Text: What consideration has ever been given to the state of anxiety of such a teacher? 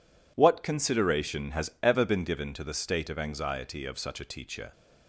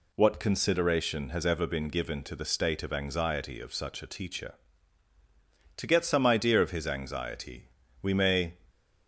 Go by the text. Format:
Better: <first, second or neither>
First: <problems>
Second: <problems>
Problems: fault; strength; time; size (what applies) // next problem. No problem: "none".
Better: first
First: none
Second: goes on to say "To get some idea of his anxiety we may"; strong; from 5.7 s on; 2.7 s long